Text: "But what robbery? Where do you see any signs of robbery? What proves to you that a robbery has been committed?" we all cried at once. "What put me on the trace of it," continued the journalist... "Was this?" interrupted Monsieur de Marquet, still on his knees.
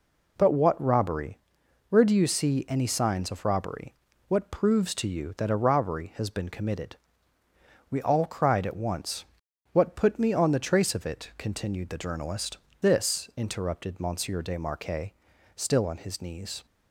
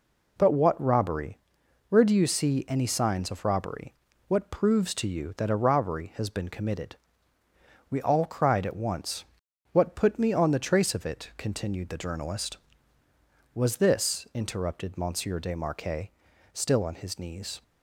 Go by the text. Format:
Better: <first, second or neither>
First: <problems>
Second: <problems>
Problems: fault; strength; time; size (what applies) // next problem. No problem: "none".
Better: second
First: skips "Was"; at 12.7 s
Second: none